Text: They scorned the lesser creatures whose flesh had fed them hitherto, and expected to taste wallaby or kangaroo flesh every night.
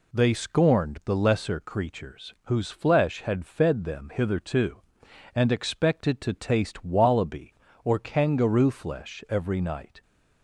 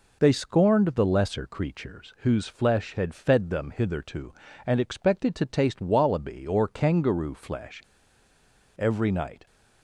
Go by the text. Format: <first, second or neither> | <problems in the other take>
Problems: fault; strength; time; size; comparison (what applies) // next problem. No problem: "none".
first | pauses between "flesh" and "every"; noticeable; at 7.8 s; 0.95 s long